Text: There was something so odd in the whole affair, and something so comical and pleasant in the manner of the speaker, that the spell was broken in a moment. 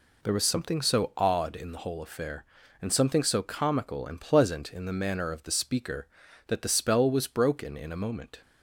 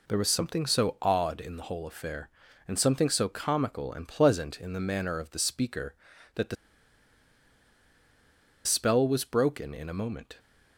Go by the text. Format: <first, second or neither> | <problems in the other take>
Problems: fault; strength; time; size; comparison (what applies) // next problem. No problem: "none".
first | pauses between "the" and "spell"; strong; at 6.5 s; 2.0 s long